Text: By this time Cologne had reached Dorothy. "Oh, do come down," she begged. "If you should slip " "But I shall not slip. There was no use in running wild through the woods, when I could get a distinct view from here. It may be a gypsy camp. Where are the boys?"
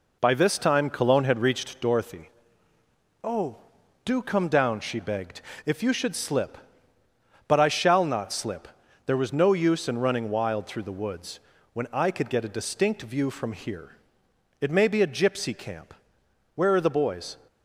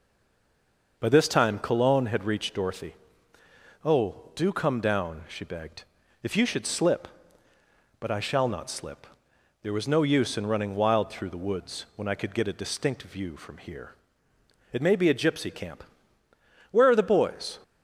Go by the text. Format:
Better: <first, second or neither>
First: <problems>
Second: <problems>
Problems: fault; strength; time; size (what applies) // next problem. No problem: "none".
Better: first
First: none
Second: stays silent before the first word; until 0.9 s; 0.9 s long